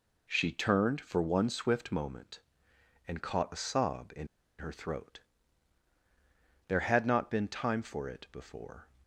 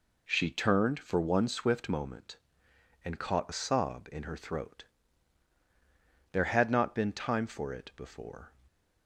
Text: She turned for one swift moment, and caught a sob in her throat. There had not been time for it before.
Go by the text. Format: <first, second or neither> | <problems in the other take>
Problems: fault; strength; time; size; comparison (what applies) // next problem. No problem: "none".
second | pauses between "in" and "her"; slight; at 4.2 s; 0.32 s long